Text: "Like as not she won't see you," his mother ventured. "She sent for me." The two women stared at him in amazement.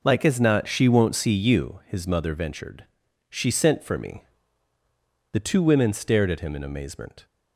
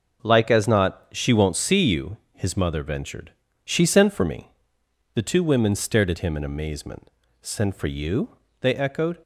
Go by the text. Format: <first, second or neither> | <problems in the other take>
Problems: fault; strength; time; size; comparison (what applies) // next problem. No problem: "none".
first | goes on to say "Sent for you they echoed"; strong; from 7.3 s on; 1.7 s long